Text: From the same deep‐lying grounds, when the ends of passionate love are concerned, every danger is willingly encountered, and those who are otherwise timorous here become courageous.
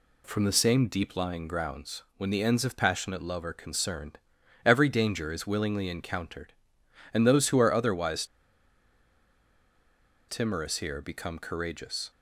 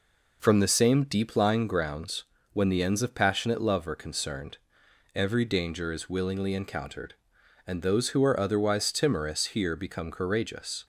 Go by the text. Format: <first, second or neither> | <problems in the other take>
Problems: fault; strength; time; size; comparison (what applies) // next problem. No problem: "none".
second | pauses between "otherwise" and "timorous"; strong; at 8.2 s; 2.0 s long